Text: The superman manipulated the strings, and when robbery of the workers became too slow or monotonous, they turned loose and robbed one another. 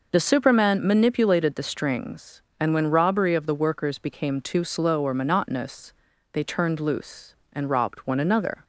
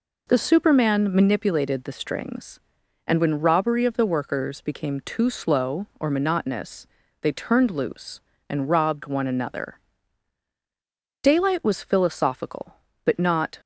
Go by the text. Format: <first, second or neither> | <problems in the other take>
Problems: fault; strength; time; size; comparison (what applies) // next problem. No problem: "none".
first | goes on to say "Daylight was philosophical but not"; strong; from 11.2 s on; 2.3 s long